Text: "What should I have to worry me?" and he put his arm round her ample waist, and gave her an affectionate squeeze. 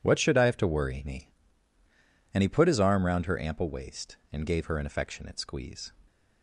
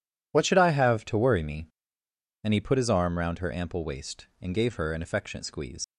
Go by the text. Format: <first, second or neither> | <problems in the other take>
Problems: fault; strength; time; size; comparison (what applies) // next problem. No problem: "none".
first | leaves "squeeze" unfinished; at 5.8 s; 80 ms